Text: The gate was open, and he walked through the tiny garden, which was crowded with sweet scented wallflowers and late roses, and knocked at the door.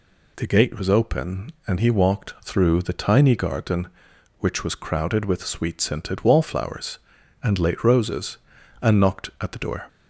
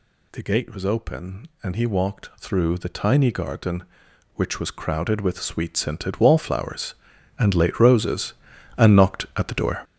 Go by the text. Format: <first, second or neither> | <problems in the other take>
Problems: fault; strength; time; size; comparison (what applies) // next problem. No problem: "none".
first | gets louder; strong; throughout; 10.5 dB